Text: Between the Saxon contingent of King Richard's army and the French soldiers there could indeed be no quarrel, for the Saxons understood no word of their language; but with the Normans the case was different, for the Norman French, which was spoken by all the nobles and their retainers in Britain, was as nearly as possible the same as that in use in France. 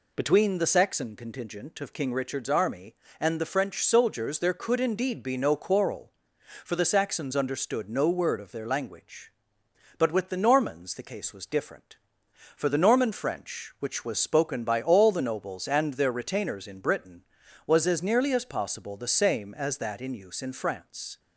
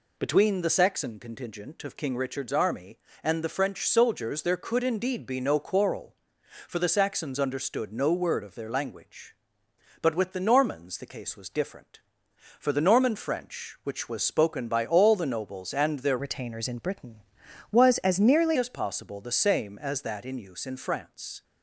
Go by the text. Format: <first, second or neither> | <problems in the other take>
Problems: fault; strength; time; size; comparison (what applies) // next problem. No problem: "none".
first | changes voice from "retainers" to "nearly"; from 16.1 to 18.5 s; 2.4 s long